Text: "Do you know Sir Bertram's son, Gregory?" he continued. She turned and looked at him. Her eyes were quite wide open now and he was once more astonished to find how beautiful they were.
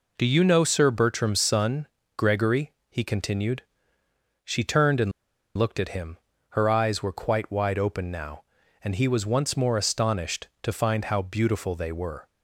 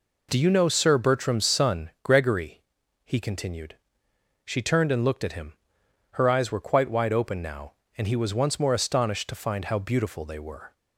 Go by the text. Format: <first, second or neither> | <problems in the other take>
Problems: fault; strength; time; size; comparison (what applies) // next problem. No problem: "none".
second | pauses between "and" and "looked"; at 5.1 s; 0.45 s long